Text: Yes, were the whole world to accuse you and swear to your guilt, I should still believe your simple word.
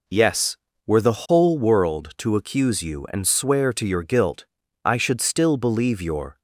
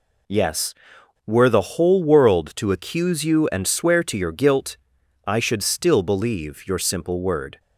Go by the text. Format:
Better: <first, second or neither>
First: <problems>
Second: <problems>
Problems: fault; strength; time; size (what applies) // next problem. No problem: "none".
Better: second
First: stops before "simple word"; at 6.3 s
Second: none